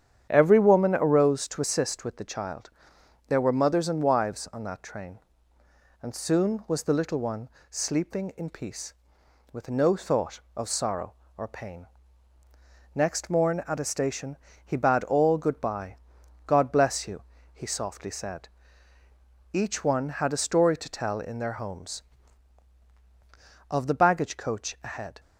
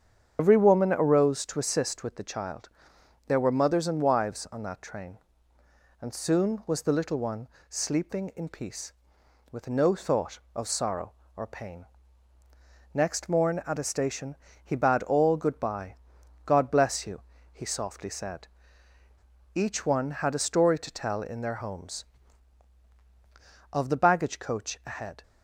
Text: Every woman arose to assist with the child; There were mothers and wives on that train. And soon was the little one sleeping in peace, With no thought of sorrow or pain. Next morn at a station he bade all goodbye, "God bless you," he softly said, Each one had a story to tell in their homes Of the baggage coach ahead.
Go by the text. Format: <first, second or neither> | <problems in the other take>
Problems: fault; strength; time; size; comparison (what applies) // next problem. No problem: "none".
first | loses the start of "Every"; at 0.3 s; 120 ms // starts louder than the rest; strong; until 1.4 s; 8 dB; strong in the first // pauses between "one" and "sleeping"; slight; at 7.4 s; 0.20 s long; slight in the first // pauses between "station" and "he"; slight; at 14.3 s; 0.26 s long; slight in the first